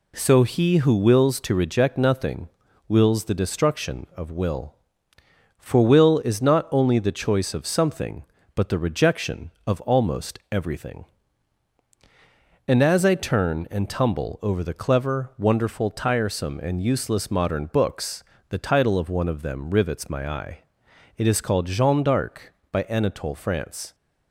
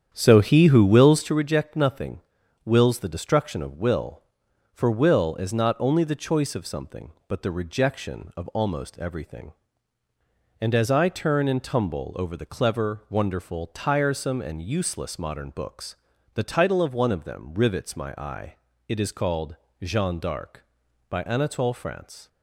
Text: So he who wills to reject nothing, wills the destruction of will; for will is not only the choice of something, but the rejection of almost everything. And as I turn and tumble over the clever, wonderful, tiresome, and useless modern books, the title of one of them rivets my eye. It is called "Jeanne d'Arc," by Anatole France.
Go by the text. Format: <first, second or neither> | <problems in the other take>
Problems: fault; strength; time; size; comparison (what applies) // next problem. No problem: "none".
first | starts louder than the rest; strong; until 1.4 s; 9 dB // pauses between "called" and "Jeanne"; slight; at 19.5 s; 0.26 s long